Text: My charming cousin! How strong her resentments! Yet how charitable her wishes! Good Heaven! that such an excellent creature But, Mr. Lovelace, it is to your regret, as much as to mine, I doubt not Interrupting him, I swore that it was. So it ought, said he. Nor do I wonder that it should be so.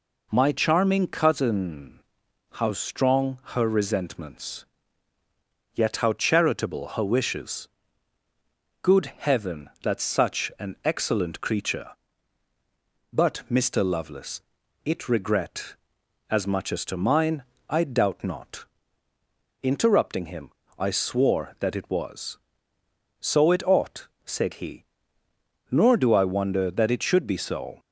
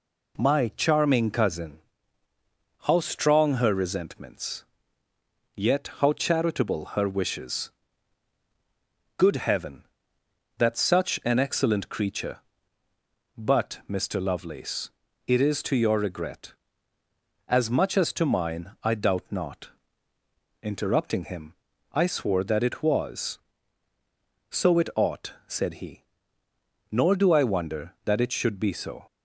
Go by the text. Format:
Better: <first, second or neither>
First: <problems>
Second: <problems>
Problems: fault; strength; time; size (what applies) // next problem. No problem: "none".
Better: second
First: skips "is to your"; at 15.0 s // pauses between "not" and "Interrupting"; noticeable; at 18.6 s; 0.98 s long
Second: pauses between "not" and "Interrupting"; noticeable; at 19.7 s; 0.92 s long